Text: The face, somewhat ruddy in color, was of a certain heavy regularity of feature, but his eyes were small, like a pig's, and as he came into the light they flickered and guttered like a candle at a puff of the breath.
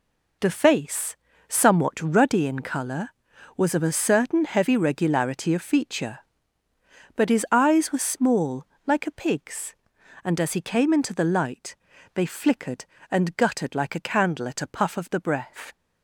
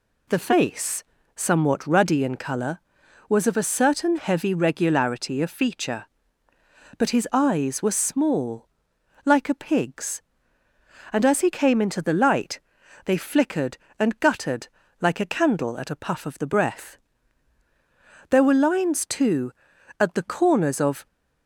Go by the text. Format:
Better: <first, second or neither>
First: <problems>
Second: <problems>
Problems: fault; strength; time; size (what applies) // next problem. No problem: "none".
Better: first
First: pauses between "light" and "they"; at 11.7 s; 0.38 s long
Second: pauses between "light" and "they"; at 12.6 s; 0.44 s long // pauses between "guttered" and "like"; slight; at 14.6 s; 0.32 s long // goes on to say "There were lines too at the corners of"; strong; from 18.2 s on; 2.7 s long